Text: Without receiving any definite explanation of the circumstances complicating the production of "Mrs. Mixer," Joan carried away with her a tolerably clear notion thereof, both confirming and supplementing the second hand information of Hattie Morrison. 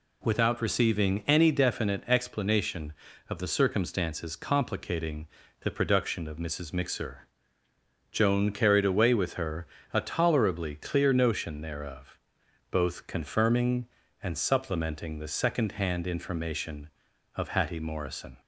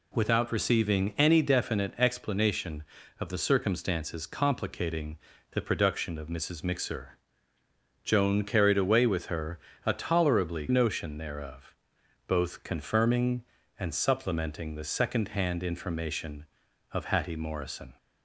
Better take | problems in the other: first | pauses between "complicating" and "the"; slight; at 5.1 s; 0.34 s long; slight in the first // pauses between "her" and "a"; slight; at 9.5 s; 0.28 s long; slight in the first // skips "clear"; at 10.6 s

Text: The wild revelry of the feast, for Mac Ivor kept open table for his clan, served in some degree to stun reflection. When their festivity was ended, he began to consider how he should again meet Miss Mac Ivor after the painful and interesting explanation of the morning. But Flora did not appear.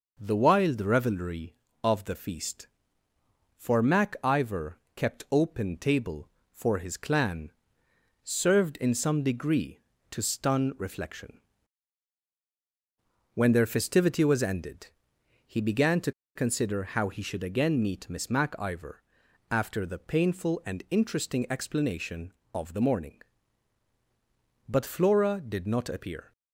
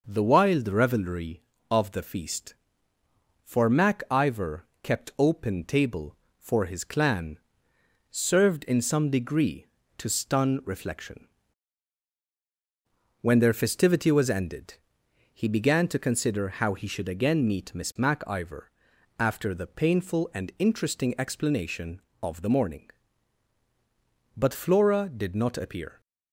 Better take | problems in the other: second | pauses between "Ivor" and "kept"; slight; at 4.7 s; 0.18 s long; slight in the second // pauses between "to" and "consider"; slight; at 16.1 s; 0.23 s long // pauses between "Ivor" and "after"; noticeable; at 19.0 s; 0.48 s long; noticeable in the second

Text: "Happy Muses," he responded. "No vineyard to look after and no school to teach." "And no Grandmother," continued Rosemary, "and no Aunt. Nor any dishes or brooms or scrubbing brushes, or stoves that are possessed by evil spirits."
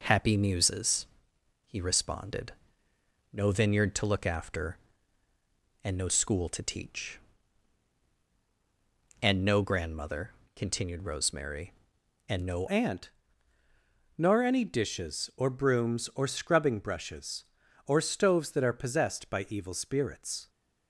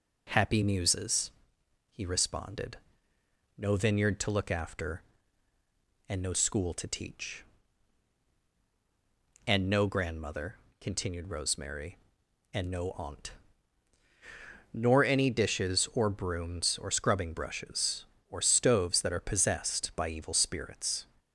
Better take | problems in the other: second | changes voice at "Aunt"; from 12.6 s on; 7.8 s long

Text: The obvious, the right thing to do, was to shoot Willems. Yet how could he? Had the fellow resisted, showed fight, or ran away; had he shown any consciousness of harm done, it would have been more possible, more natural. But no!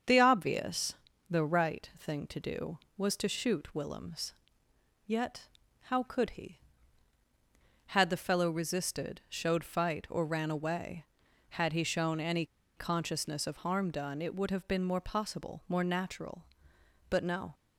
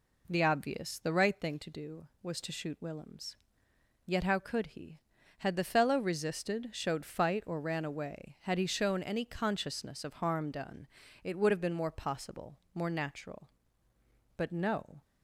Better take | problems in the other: second | starts louder than the rest; until 1.4 s; 7 dB // pauses between "Yet" and "how"; slight; at 5.4 s; 0.36 s long // pauses between "any" and "consciousness"; slight; at 12.4 s; 0.32 s long

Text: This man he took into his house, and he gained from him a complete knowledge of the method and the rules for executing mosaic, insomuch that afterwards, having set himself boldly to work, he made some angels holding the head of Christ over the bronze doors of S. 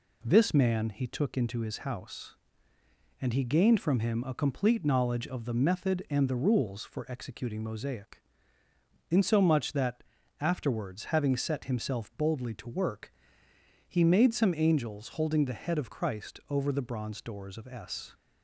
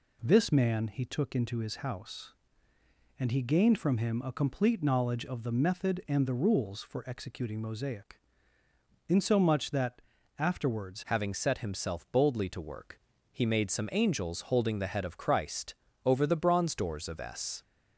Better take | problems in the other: first | pauses between "that" and "afterwards"; slight; at 10.0 s; 0.36 s long; slight in the first // changes voice at "having"; from 11.0 s on; 6.6 s long // pauses between "Christ" and "over"; slight; at 15.7 s; 0.28 s long

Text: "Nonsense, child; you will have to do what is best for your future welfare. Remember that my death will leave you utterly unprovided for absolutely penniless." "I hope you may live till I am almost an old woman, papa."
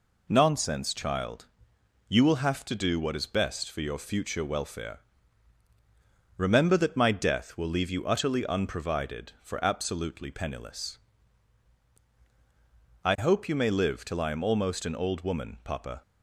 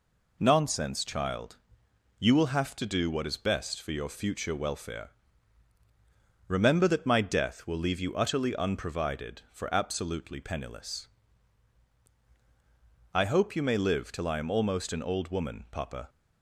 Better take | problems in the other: neither | none

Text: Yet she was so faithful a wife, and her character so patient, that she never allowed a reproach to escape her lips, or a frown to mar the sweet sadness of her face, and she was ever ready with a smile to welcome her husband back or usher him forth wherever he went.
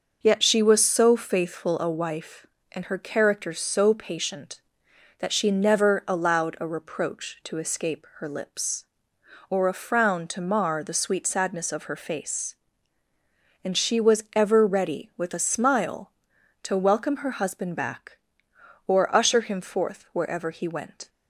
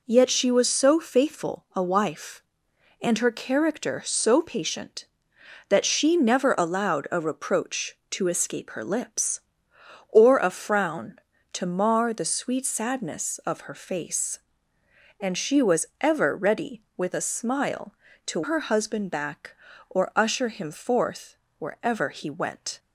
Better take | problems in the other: first | pauses between "was" and "ever"; slight; at 15.8 s; 0.16 s long // skips "welcome"; at 18.4 s // pauses between "forth" and "wherever"; slight; at 21.3 s; 0.24 s long

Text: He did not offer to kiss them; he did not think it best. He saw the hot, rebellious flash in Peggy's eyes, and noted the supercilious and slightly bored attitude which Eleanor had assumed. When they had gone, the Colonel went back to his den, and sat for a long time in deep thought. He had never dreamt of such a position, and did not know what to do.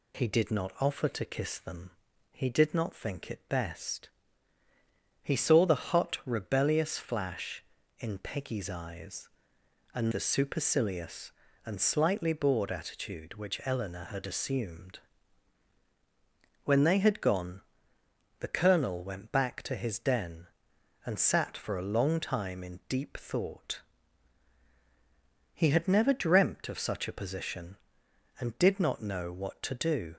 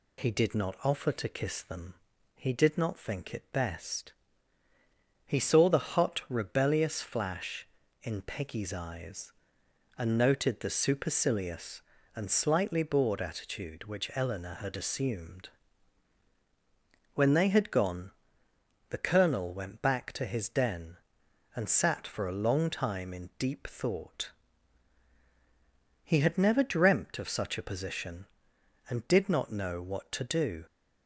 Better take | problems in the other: second | skips "noted"; at 10.1 s

